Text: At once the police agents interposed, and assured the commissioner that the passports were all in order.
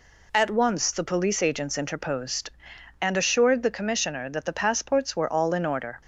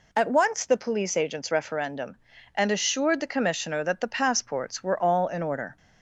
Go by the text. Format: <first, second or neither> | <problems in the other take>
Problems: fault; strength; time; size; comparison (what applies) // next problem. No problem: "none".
first | says "referendum" for "interposed"; at 1.5 s